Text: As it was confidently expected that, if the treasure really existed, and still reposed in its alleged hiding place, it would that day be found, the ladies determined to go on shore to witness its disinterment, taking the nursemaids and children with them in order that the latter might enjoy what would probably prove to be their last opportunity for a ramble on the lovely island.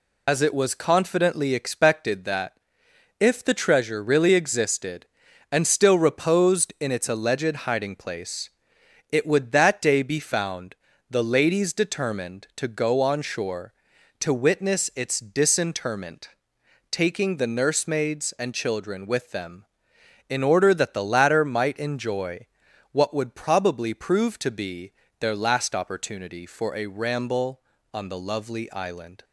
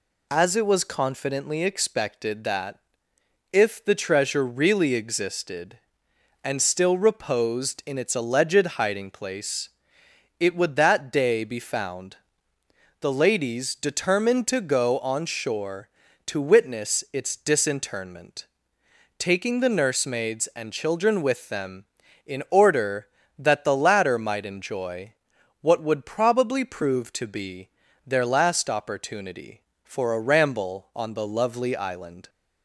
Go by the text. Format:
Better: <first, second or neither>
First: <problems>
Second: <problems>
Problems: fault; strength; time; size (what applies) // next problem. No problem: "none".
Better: second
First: loses the start of "As"; at 0.2 s; 60 ms // pauses between "enjoy" and "what"; noticeable; at 22.4 s; 0.46 s long // pauses between "be" and "their"; slight; at 24.9 s; 0.28 s long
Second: pauses between "enjoy" and "what"; noticeable; at 25.1 s; 0.48 s long // pauses between "be" and "their"; slight; at 27.6 s; 0.36 s long